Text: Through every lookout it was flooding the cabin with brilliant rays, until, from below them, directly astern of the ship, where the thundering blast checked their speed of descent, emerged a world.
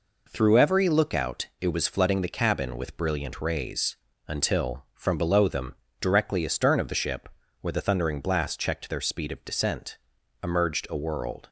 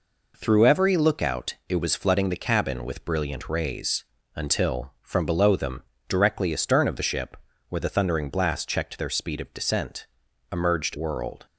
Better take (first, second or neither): first